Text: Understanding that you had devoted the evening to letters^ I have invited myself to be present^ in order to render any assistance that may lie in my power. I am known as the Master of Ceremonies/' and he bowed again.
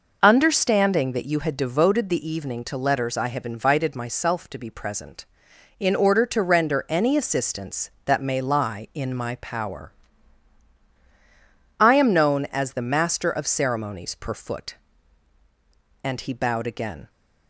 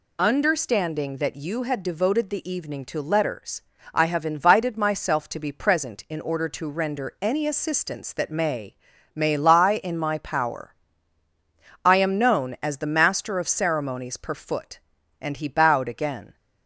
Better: first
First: none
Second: pauses between "letters" and "I"; slight; at 3.6 s; 0.30 s long // says "may" twice; at 9.1 s

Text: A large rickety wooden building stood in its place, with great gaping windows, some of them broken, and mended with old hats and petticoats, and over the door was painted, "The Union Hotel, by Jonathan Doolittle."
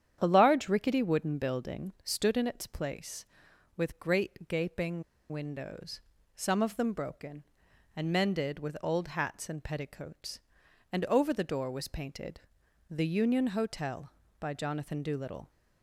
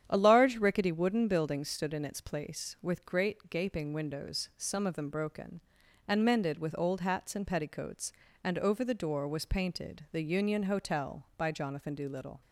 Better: second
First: starts louder than the rest; strong; until 1.2 s; 9.5 dB // pauses between "gaping" and "windows"; slight; at 5.0 s; 0.29 s long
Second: starts louder than the rest; strong; until 1.0 s; 9 dB

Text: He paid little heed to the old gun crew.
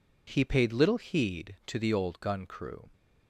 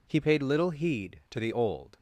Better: first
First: none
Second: stops before "gun crew"; at 1.9 s

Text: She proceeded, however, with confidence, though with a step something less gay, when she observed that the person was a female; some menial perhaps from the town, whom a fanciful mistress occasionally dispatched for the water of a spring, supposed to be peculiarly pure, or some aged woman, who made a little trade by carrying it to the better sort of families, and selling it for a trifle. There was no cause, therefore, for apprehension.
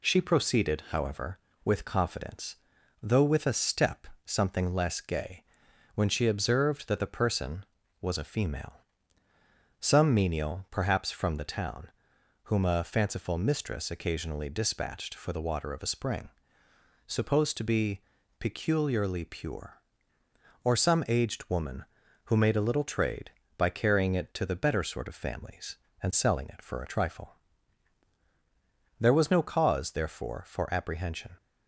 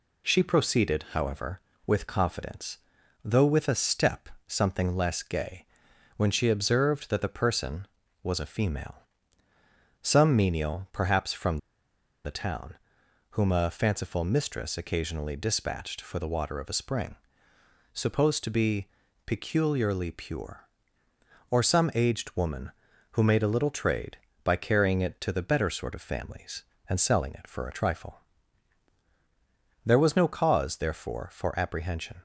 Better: first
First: pauses between "step" and "something"; slight; at 4.0 s; 0.20 s long // pauses between "be" and "peculiarly"; at 18.0 s; 0.38 s long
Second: pauses between "step" and "something"; slight; at 4.2 s; 0.20 s long // pauses between "from" and "the"; noticeable; at 11.5 s; 0.67 s long // pauses between "be" and "peculiarly"; at 18.8 s; 0.38 s long

